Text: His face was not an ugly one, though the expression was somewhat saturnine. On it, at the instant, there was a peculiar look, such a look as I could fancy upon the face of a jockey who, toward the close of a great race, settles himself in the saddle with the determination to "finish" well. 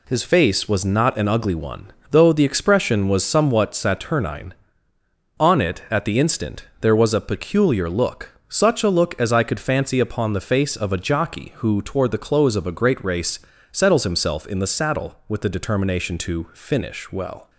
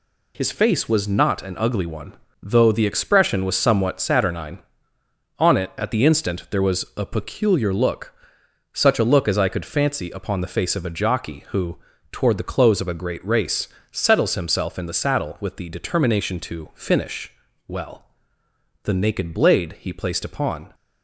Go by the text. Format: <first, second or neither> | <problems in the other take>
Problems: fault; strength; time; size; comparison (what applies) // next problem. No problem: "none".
first | pauses between "finish" and "well"; slight; at 17.3 s; 0.34 s long // goes on to say "The naked blade he placed upon"; strong; from 18.8 s on; 1.9 s long